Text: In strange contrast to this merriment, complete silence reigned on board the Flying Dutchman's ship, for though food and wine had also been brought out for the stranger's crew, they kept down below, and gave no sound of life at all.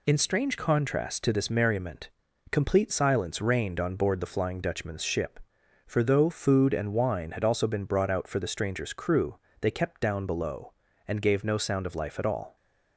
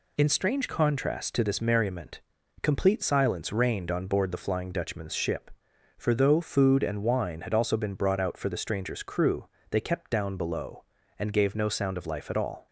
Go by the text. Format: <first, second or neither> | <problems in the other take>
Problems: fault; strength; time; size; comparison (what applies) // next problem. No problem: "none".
neither | none